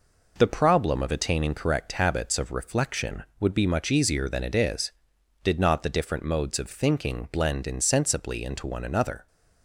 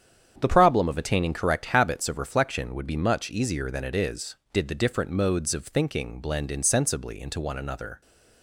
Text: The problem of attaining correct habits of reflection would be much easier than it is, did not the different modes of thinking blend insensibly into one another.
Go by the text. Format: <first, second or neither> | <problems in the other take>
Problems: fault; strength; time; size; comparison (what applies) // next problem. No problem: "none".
first | starts louder than the rest; strong; until 1.3 s; 8.5 dB // skips "not"; at 4.6 s